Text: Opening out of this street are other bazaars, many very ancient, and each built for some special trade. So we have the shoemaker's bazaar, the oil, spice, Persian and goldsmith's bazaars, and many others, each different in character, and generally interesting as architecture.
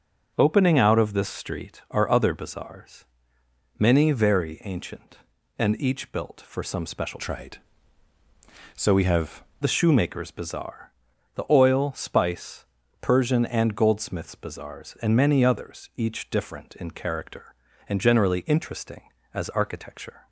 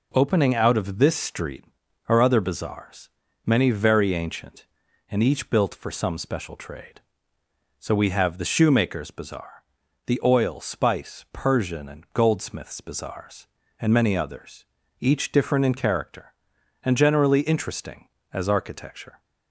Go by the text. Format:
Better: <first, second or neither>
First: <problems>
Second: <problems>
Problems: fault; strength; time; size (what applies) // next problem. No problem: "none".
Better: second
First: starts louder than the rest; until 1.3 s; 6.5 dB // changes voice from "trade" to "have"; from 7.1 to 9.4 s; 2.3 s long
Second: none